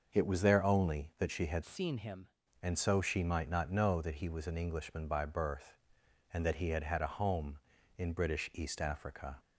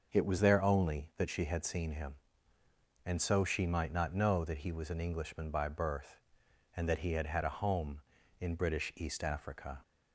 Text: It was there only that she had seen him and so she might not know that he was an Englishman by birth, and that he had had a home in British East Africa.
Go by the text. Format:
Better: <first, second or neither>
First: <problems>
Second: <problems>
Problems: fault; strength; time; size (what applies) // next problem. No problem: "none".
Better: second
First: starts louder than the rest; noticeable; until 1.1 s; 6 dB // changes voice from "seen" to "him"; from 1.6 to 2.2 s; 0.6 s long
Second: starts louder than the rest; until 1.1 s; 6.5 dB